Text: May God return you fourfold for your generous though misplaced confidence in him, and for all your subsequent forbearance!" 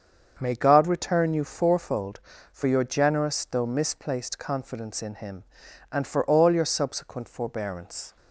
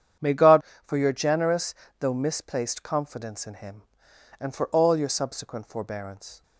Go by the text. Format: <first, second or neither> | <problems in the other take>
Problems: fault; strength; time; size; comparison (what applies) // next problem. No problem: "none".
first | starts louder than the rest; strong; until 1.4 s; 8.5 dB; also in the first // skips "return you fourfold"; at 0.7 s // pauses between "generous" and "though"; slight; at 1.7 s; 0.26 s long